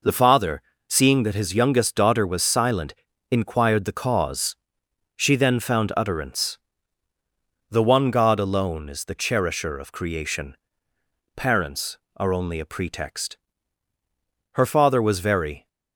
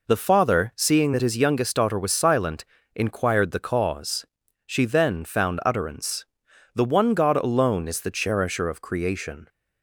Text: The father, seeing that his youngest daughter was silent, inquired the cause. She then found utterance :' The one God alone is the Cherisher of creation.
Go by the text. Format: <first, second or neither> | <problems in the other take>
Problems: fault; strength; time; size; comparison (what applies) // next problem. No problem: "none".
second | goes on to say "Parents are only a pretext Her father was very"; strong; from 11.3 s on; 4.3 s long